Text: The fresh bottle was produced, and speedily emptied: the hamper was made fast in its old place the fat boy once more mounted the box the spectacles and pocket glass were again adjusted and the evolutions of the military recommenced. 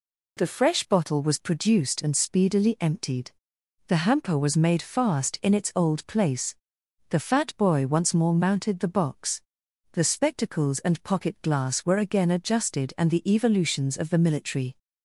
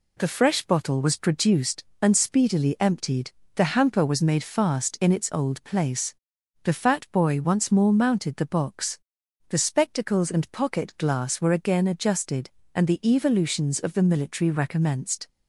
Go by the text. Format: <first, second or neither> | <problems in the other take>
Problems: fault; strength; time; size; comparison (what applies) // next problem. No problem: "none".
second | pauses between "place" and "the"; noticeable; at 6.5 s; 0.56 s long; noticeable in the second // pauses between "box" and "the"; noticeable; at 9.4 s; 0.52 s long; noticeable in the second // stops before "recommenced"; at 14.7 s